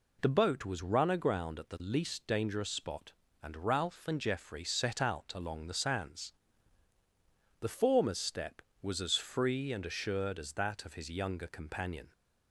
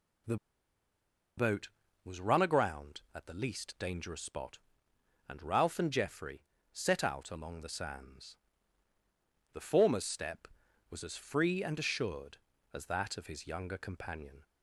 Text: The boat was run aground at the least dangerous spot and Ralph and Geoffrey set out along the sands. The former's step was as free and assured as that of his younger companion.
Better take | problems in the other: first | pauses between "The" and "boat"; at 0.3 s; 1.0 s long // pauses between "Geoffrey" and "set"; slight; at 6.4 s; 0.30 s long

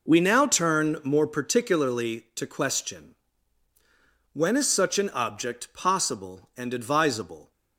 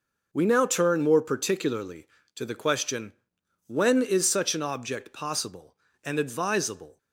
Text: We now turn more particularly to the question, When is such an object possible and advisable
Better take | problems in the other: second | skips "the"; at 2.4 s

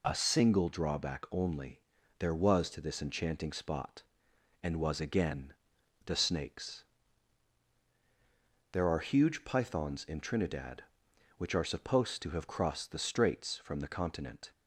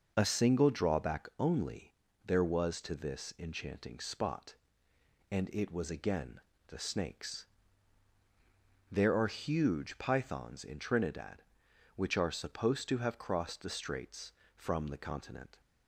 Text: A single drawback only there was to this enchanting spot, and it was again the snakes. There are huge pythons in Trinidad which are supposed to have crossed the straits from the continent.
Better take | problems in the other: second | pauses between "only" and "there"; at 1.7 s; 0.40 s long; slight in the second // skips "it"; at 4.7 s // pauses between "again" and "the"; noticeable; at 5.5 s; 0.54 s long; slight in the second

